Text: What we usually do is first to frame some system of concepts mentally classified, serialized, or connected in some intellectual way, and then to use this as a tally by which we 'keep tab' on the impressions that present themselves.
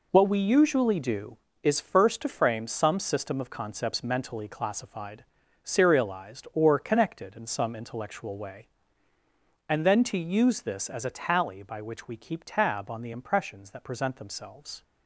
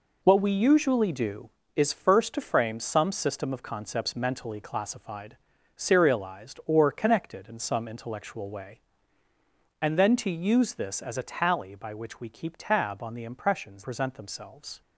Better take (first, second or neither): first